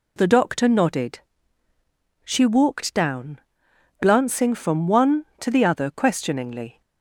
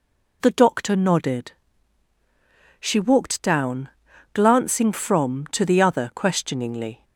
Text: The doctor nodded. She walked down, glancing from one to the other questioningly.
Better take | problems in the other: first | skips "one"; at 5.4 s

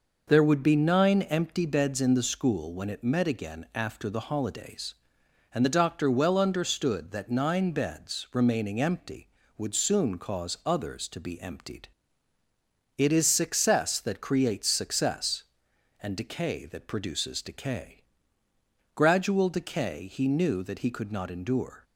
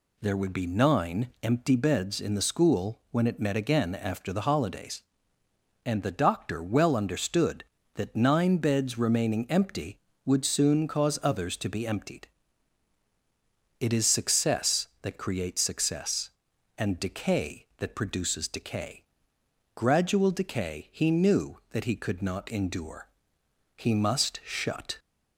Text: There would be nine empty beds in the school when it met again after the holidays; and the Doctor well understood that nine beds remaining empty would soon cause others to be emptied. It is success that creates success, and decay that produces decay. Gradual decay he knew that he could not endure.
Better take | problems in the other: first | goes on to say "He must shut"; noticeable; from 23.7 s on; 1.2 s long

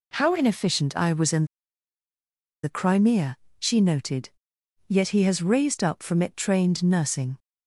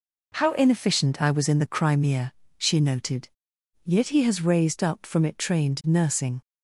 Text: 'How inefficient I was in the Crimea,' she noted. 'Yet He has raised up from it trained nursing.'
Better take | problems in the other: second | pauses between "in" and "the"; at 1.4 s; 1.1 s long

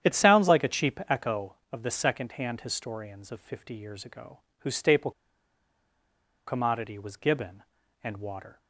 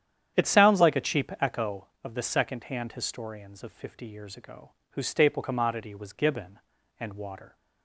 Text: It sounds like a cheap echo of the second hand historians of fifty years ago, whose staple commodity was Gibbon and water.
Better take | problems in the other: second | starts louder than the rest; strong; until 1.1 s; 10 dB; strong in the second // pauses between "staple" and "commodity"; strong; at 5.1 s; 1.3 s long

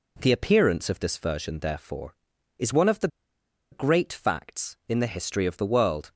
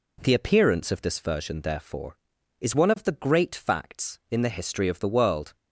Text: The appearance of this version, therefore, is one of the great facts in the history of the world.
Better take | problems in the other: second | pauses between "the" and "great"; noticeable; at 3.0 s; 0.64 s long

